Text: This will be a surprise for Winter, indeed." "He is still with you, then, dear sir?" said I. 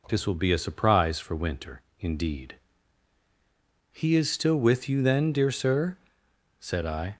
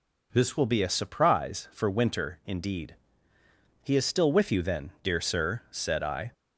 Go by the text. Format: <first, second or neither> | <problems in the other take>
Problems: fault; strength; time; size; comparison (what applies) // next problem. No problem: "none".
first | changes voice at "will"; from 0.5 s on; 5.8 s long